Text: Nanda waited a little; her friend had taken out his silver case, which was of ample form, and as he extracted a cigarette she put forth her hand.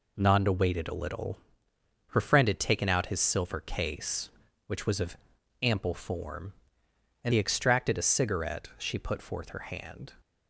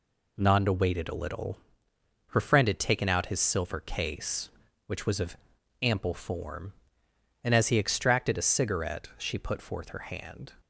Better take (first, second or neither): second